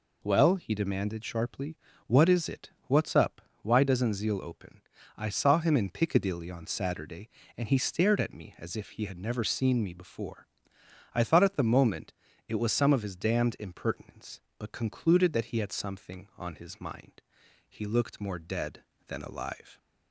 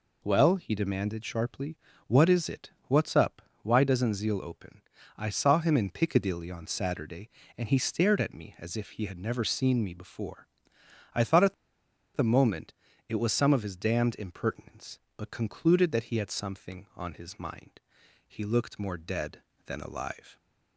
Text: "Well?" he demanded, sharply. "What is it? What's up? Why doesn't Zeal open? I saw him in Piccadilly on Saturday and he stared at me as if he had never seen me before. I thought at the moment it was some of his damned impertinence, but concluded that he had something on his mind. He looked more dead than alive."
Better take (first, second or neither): first